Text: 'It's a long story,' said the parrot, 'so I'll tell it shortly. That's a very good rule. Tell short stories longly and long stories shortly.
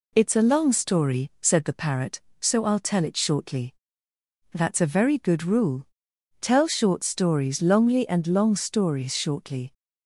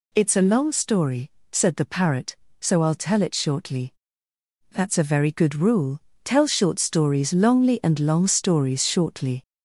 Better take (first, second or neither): first